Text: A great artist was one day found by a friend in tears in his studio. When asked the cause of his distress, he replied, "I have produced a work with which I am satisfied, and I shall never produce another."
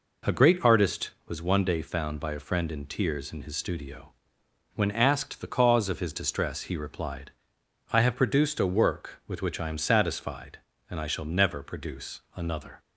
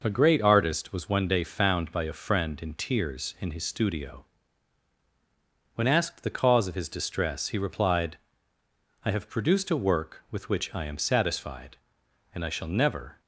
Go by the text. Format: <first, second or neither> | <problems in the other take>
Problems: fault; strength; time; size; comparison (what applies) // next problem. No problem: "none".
first | stops before "produce another"; at 13.2 s